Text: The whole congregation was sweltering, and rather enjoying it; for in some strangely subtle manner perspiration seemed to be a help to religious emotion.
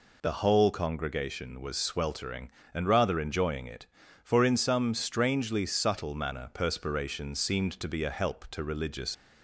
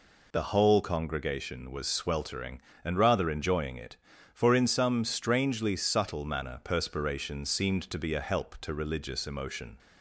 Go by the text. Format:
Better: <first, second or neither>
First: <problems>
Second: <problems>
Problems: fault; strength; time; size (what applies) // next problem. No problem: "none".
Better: second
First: stops before "emotion"; at 9.1 s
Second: none